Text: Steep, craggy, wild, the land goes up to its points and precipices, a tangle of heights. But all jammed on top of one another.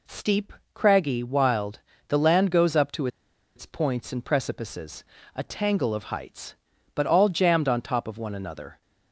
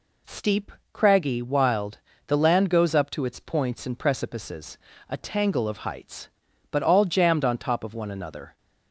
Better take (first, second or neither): second